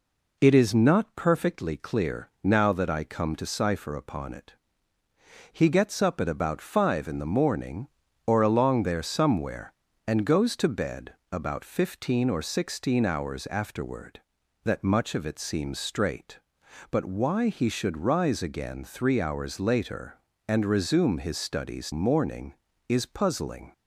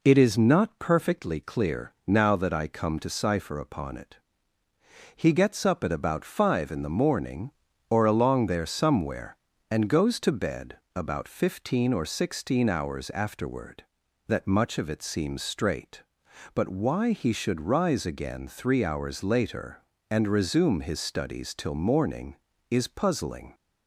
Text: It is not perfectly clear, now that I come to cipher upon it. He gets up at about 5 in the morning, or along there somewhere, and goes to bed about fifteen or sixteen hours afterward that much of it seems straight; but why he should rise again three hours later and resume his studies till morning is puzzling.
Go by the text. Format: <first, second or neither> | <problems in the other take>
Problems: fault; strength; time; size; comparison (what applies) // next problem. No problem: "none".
second | pauses between "bed" and "about"; slight; at 11.1 s; 0.18 s long; slight in the second // skips "till"; at 21.9 s